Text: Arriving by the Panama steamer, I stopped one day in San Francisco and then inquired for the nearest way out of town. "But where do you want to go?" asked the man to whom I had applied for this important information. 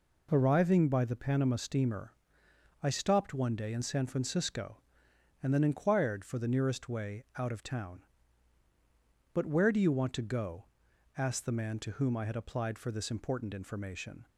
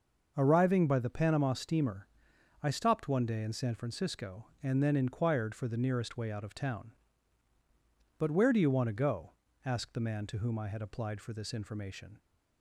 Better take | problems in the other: first | starts louder than the rest; noticeable; until 1.3 s; 6 dB // skips "important"; at 11.5 s

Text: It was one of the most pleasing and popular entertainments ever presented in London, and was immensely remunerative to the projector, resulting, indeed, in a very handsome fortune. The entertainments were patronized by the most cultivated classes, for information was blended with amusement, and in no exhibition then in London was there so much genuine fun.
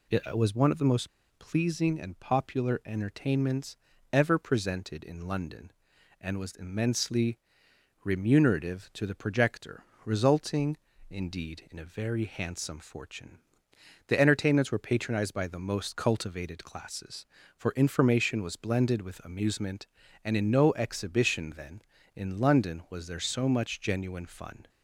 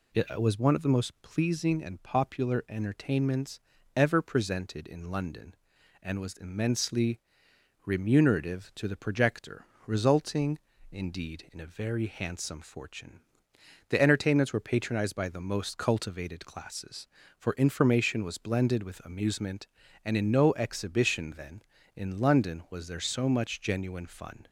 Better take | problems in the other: second | pauses between "most" and "pleasing"; slight; at 1.0 s; 0.29 s long // pauses between "entertainments" and "ever"; slight; at 3.7 s; 0.36 s long; slight in the second // pauses between "immensely" and "remunerative"; noticeable; at 7.3 s; 0.66 s long; noticeable in the second

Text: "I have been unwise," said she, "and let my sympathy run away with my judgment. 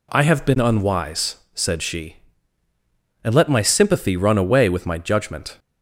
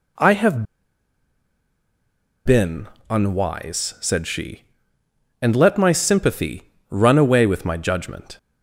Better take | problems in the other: first | pauses between "have" and "been"; strong; at 0.6 s; 1.8 s long // pauses between "been" and "unwise"; slight; at 2.8 s; 0.20 s long // pauses between "sympathy" and "run"; slight; at 6.6 s; 0.20 s long

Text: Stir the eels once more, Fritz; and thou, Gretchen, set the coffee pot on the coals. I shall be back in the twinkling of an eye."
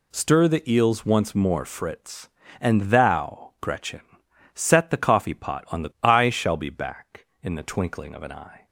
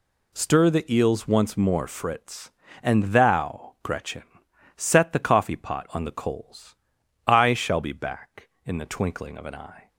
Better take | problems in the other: second | skips "coals"; at 5.9 s

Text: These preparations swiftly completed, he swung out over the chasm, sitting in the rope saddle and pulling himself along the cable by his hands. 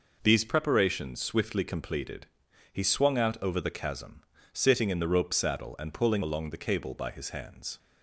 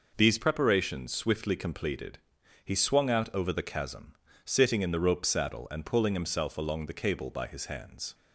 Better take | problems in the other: second | skips "himself"; at 6.2 s

